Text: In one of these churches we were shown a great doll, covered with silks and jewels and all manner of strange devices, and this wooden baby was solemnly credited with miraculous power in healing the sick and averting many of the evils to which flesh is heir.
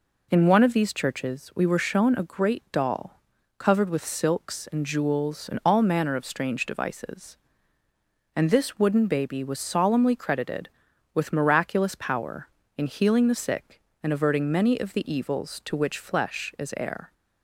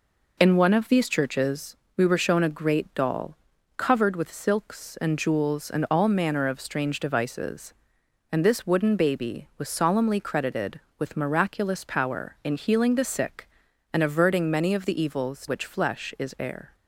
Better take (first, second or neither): first